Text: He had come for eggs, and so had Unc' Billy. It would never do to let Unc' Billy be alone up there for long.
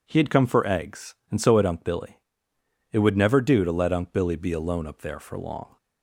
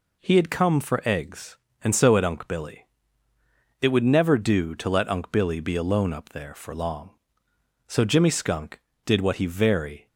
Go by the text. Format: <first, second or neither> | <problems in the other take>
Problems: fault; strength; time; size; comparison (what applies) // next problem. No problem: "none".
first | goes on to say "So Jimmy Skunk did what he very"; strong; from 7.8 s on; 2.2 s long